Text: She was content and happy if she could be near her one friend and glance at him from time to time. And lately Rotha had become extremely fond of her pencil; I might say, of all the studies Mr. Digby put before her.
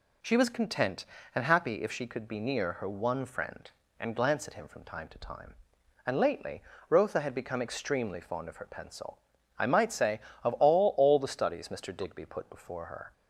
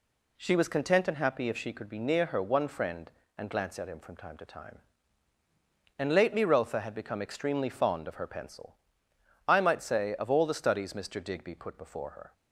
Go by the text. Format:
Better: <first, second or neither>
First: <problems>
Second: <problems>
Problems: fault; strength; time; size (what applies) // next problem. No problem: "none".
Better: second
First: pauses between "lately" and "Rotha"; slight; at 6.6 s; 0.26 s long // says "all" twice; at 10.9 s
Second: none